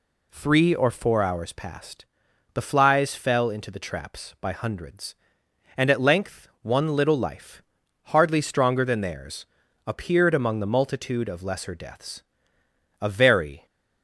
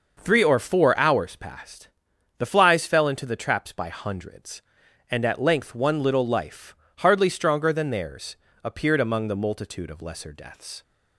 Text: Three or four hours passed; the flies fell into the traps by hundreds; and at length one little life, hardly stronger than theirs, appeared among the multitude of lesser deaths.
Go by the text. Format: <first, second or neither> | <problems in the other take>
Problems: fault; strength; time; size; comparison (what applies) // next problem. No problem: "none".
second | goes on to say "A very"; noticeable; from 13.0 s on; 0.64 s long